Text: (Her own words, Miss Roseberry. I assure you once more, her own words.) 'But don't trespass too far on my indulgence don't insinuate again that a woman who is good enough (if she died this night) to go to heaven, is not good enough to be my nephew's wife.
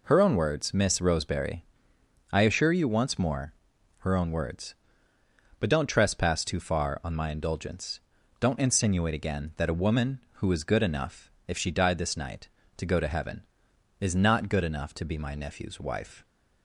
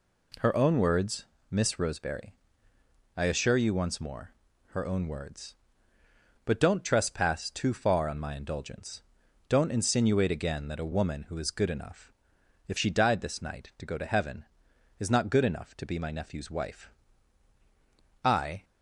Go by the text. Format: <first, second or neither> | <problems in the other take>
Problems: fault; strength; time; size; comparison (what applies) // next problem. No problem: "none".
first | pauses between "indulgence" and "don't"; noticeable; at 9.0 s; 0.46 s long; also in the first // goes on to say "I"; slight; from 18.2 s on; 0.40 s long